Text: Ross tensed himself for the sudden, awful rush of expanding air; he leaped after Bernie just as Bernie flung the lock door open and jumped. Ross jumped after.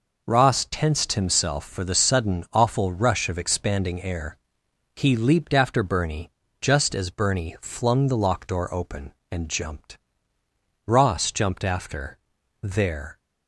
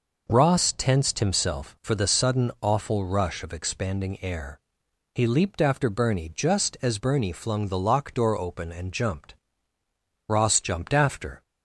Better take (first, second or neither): second